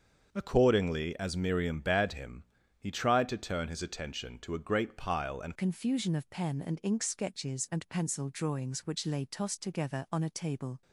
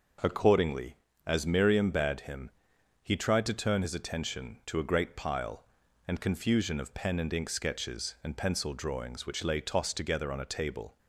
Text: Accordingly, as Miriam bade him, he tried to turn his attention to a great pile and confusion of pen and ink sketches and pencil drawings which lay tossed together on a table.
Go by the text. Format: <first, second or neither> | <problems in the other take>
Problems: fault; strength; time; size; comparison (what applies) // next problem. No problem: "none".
second | starts louder than the rest; until 1.3 s; 7 dB // changes voice at "confusion"; from 5.5 s on; 5.3 s long